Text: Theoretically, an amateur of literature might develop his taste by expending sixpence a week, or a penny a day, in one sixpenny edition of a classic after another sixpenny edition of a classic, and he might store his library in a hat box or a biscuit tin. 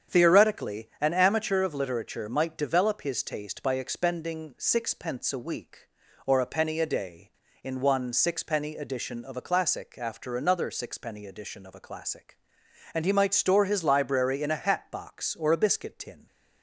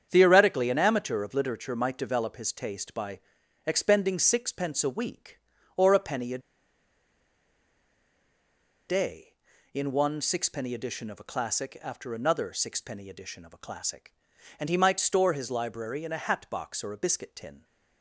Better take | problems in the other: first | starts louder than the rest; strong; until 1.1 s; 8 dB; strong in the first // pauses between "by" and "expending"; noticeable; at 3.2 s; 0.46 s long // pauses between "a" and "day"; strong; at 6.3 s; 2.5 s long

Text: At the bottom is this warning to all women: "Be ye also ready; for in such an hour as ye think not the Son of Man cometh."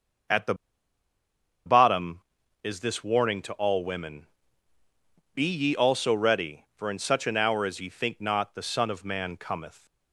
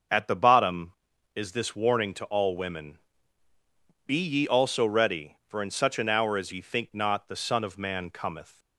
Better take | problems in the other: second | starts louder than the rest; until 2.8 s; 6.5 dB; also in the second // pauses between "the" and "bottom"; at 0.5 s; 1.1 s long

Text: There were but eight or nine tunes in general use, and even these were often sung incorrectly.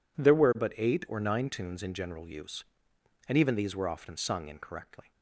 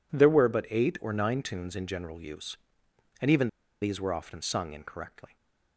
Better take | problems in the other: first | pauses between "even" and "these"; slight; at 3.4 s; 0.34 s long // stays silent after the last word; slight; from 5.2 s on; 0.5 s long

